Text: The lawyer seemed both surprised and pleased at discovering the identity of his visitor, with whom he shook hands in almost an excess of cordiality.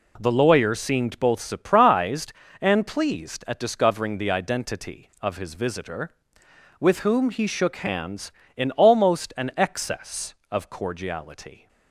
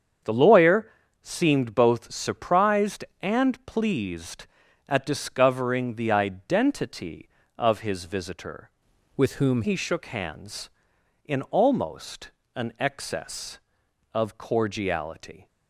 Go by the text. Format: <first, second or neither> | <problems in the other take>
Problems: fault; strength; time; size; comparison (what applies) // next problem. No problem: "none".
first | starts louder than the rest; strong; until 1.5 s; 7.5 dB // pauses between "lawyer" and "seemed"; slight; at 0.8 s; 0.32 s long // changes voice from "with" to "whom"; from 9.1 to 9.6 s; 0.5 s long // pauses between "almost" and "an"; slight; at 12.3 s; 0.24 s long